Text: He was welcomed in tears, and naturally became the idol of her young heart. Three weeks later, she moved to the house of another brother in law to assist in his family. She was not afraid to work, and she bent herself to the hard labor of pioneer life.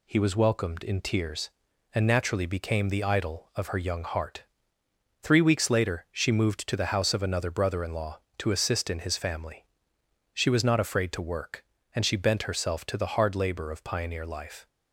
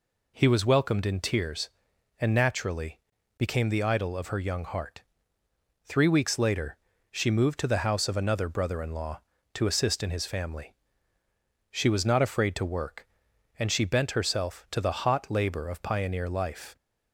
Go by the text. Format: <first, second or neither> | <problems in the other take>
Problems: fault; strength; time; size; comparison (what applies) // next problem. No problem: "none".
first | pauses between "naturally" and "became"; at 2.9 s; 0.40 s long // says "hot" for "hard"; at 15.0 s